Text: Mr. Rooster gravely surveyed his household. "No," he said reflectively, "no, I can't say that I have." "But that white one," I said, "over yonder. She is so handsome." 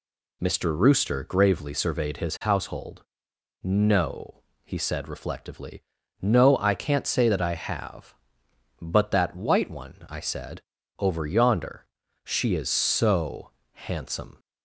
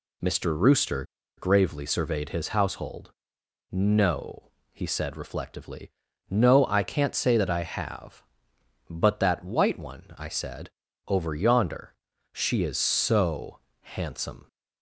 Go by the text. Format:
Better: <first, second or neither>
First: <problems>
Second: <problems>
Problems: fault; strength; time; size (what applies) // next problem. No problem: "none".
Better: first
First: pauses between "so" and "handsome"; slight; at 13.5 s; 0.20 s long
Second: pauses between "Rooster" and "gravely"; slight; at 1.0 s; 0.33 s long // pauses between "so" and "handsome"; slight; at 13.5 s; 0.20 s long